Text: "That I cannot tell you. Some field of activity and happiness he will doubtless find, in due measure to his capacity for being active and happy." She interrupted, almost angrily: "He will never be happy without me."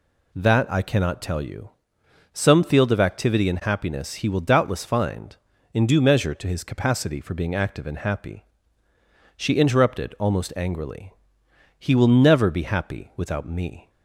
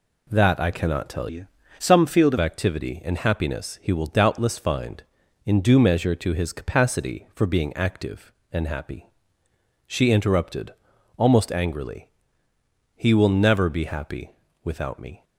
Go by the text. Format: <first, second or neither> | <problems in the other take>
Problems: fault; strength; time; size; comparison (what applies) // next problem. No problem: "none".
first | changes voice from "you" to "of"; from 1.2 to 2.3 s; 1.1 s long // pauses between "happy" and "without"; slight; at 14.3 s; 0.32 s long